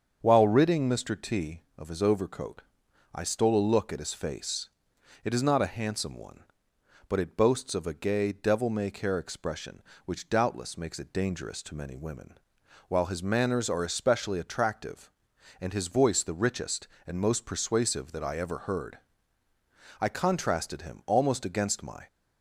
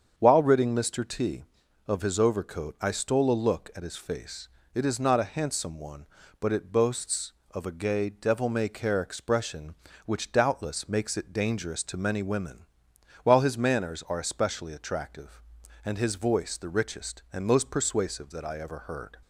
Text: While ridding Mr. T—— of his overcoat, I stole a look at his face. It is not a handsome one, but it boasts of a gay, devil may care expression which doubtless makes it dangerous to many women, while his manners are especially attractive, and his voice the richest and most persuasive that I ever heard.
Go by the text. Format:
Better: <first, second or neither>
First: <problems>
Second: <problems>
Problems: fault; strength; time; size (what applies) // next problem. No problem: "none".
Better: second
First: starts louder than the rest; strong; until 1.2 s; 7.5 dB // goes on to say "I contrasted him almost against my"; strong; from 20.0 s on; 2.0 s long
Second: starts louder than the rest; strong; until 1.1 s; 7 dB